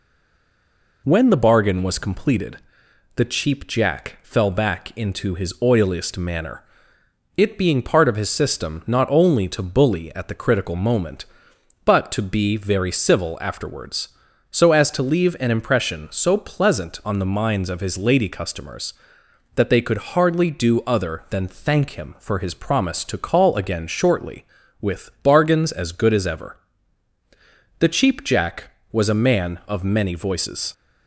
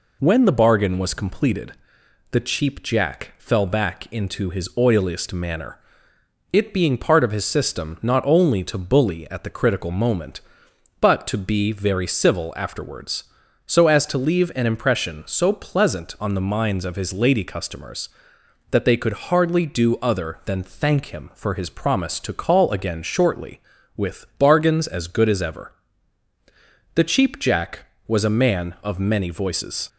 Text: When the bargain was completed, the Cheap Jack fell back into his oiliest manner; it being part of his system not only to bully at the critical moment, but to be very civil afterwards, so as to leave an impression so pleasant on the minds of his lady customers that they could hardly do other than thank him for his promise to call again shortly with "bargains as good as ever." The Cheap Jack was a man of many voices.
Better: second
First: stays silent before the first word; until 1.0 s; 1.0 s long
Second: none

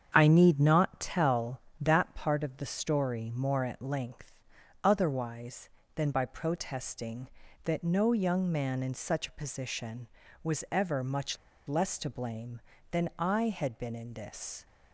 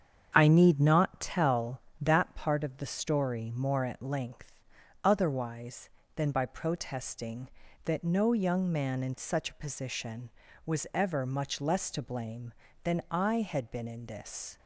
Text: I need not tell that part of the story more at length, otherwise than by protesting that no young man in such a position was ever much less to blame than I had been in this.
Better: second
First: starts louder than the rest; strong; until 1.1 s; 7.5 dB // pauses between "much" and "less"; slight; at 11.3 s; 0.32 s long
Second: starts louder than the rest; strong; until 1.3 s; 7.5 dB

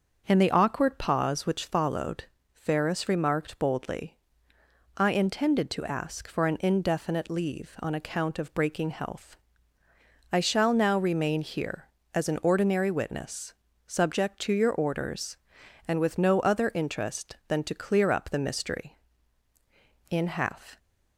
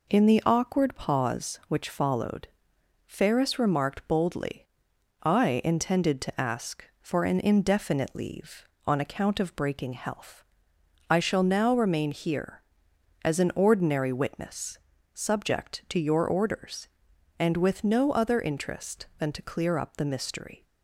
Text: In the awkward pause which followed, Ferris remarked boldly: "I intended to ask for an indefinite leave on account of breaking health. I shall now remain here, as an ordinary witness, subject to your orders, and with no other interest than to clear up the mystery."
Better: second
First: starts louder than the rest; until 1.2 s; 6.5 dB // goes on to say "In half"; noticeable; from 20.0 s on; 0.68 s long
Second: none

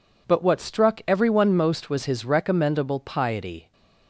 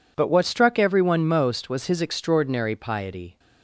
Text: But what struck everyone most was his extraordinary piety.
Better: second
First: says "recommendable" for "extraordinary"; at 2.2 s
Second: none

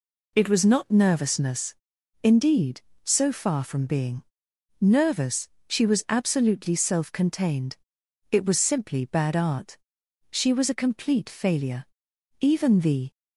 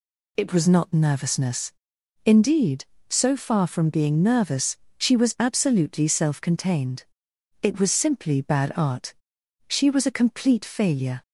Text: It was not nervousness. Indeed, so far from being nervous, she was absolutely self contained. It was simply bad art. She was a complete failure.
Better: second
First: pauses between "being" and "nervous"; noticeable; at 4.2 s; 0.56 s long // goes on to say "Even the"; noticeable; from 12.4 s on; 0.70 s long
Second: none

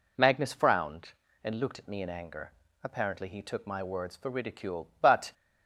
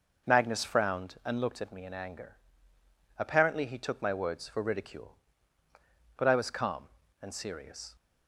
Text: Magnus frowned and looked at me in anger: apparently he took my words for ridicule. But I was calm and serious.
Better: second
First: stops before "I was calm and serious"; at 5.3 s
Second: none

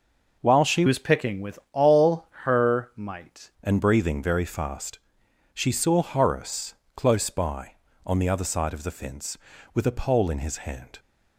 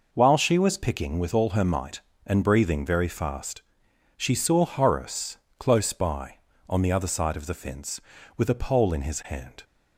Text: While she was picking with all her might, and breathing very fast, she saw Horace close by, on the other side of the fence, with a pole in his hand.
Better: second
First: changes voice from "was" to "might"; from 0.8 to 3.5 s; 2.7 s long // pauses between "all" and "her"; slight; at 2.2 s; 0.16 s long // pauses between "Horace" and "close"; slight; at 6.7 s; 0.20 s long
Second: pauses between "Horace" and "close"; slight; at 5.3 s; 0.20 s long

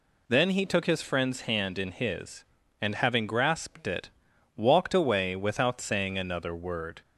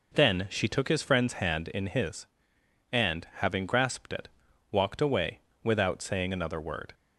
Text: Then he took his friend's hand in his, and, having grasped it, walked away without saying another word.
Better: first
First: none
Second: says "she" for "he"; at 0.5 s // pauses between "away" and "without"; slight; at 5.4 s; 0.22 s long

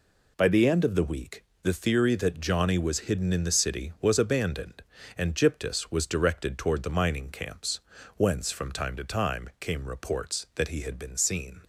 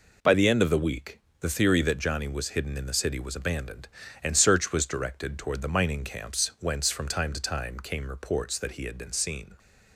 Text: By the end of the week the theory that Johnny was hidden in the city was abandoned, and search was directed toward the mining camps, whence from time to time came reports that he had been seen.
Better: second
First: pauses between "week" and "the"; slight; at 1.4 s; 0.18 s long // says "gyptus" for "search"; at 5.3 s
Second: pauses between "week" and "the"; slight; at 1.1 s; 0.24 s long

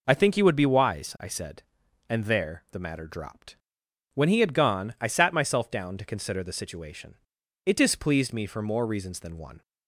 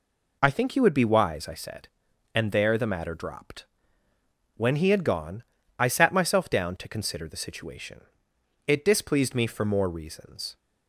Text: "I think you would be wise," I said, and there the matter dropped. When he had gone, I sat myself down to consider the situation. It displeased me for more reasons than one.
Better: first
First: none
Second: stops before "than one"; at 10.5 s

